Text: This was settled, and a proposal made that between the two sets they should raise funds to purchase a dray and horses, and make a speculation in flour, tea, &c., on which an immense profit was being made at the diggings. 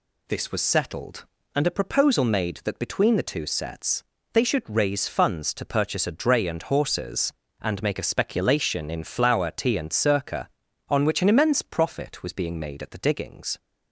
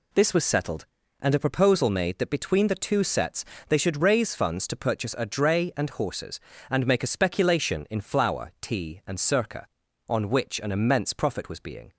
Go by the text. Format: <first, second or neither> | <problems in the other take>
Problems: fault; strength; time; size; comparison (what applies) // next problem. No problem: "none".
first | pauses between "sets" and "they"; slight; at 3.4 s; 0.24 s long; slight in the first // stops before "made at the diggings"; at 11.9 s